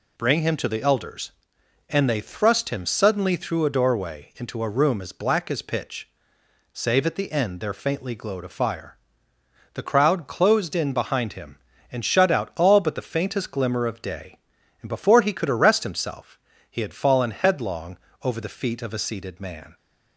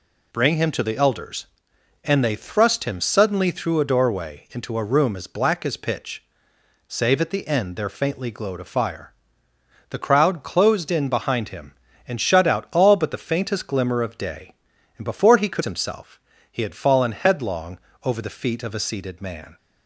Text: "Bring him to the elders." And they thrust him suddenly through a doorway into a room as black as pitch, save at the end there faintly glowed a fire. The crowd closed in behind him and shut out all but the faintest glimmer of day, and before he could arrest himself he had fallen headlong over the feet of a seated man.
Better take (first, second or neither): first